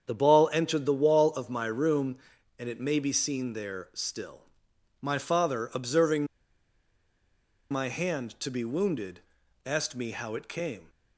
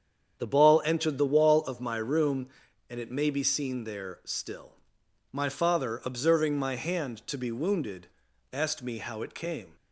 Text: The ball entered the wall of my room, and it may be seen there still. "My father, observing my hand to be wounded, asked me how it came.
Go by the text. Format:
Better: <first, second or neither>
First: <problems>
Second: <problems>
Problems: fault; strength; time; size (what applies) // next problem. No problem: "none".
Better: second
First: starts louder than the rest; strong; until 1.0 s; 8 dB // pauses between "observing" and "my"; strong; at 6.2 s; 1.4 s long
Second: starts louder than the rest; strong; until 1.4 s; 8 dB